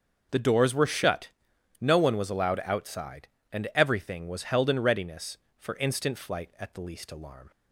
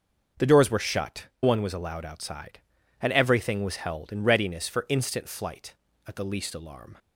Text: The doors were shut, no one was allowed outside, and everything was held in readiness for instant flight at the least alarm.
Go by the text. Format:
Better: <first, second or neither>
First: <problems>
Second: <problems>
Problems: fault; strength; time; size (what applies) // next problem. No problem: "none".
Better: first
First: starts louder than the rest; until 1.8 s; 6.5 dB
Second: starts louder than the rest; until 1.5 s; 6.5 dB // skips "no"; at 1.3 s